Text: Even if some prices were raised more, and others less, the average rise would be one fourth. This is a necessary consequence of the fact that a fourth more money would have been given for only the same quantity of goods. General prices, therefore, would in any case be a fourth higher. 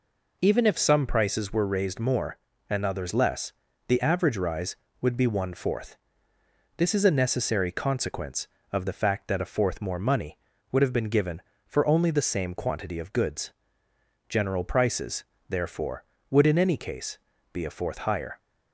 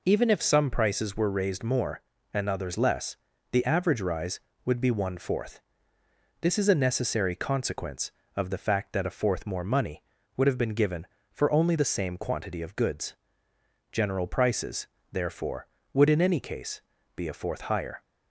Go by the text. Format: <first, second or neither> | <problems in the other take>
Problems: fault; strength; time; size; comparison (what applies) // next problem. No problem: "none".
neither | pauses between "case" and "be"; slight; the same in both